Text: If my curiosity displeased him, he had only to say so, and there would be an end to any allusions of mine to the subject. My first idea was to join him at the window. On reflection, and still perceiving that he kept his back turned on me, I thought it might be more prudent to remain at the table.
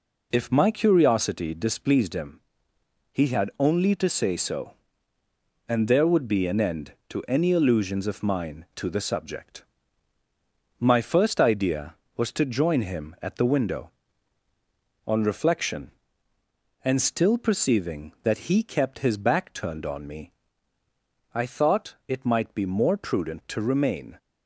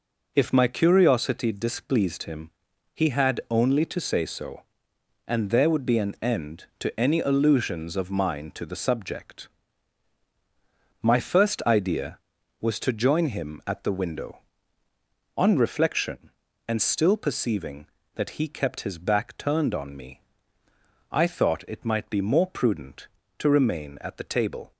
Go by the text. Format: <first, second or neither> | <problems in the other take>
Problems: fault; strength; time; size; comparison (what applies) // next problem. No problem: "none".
second | stops before "at the table"; at 24.1 s